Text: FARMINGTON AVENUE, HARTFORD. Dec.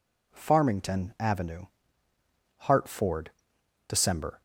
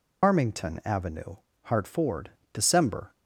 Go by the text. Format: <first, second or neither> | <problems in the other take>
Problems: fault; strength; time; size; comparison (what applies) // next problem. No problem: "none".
first | loses the start of "FARMINGTON"; at 0.2 s; 170 ms